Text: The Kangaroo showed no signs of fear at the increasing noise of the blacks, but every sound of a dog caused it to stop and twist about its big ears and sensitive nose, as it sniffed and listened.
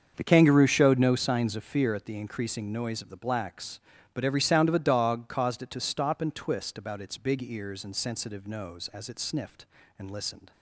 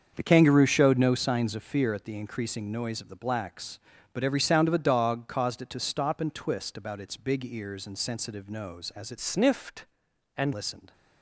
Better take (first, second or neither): first